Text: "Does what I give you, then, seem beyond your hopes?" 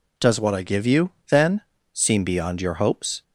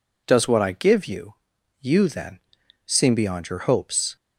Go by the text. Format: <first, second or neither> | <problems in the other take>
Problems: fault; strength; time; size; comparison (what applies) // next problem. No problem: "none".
first | says "you" twice; at 1.8 s